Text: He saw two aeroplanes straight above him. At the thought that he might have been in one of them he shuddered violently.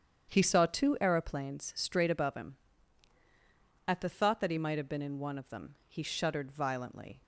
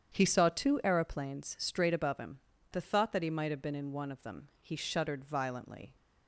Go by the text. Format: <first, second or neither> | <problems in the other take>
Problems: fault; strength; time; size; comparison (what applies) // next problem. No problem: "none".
first | starts louder than the rest; strong; until 1.1 s; 8.5 dB; strong in the first // skips "At"; at 2.5 s